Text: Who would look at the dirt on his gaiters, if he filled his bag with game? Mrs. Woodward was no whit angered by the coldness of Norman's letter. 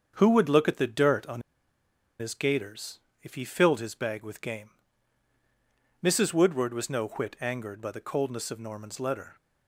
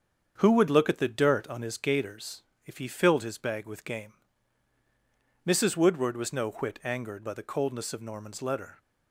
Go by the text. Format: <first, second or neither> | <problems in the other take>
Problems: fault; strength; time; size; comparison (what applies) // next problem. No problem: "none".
second | starts louder than the rest; strong; until 1.1 s; 7 dB; also in the second // pauses between "on" and "his"; noticeable; at 1.4 s; 0.79 s long